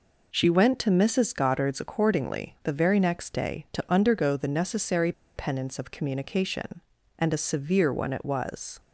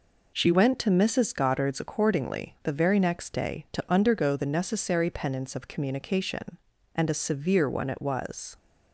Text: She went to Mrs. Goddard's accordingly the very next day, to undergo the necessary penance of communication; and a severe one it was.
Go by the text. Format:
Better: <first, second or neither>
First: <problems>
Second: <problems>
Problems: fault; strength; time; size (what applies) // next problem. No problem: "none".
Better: second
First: pauses between "necessary" and "penance"; slight; at 5.1 s; 0.24 s long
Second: none